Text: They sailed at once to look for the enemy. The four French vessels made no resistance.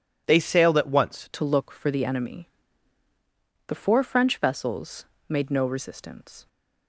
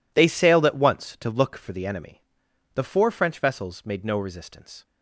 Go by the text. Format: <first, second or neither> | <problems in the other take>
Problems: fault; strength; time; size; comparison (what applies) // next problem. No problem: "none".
second | changes voice at "to"; from 1.3 s on; 5.1 s long // pauses between "vessels" and "made"; slight; at 5.0 s; 0.22 s long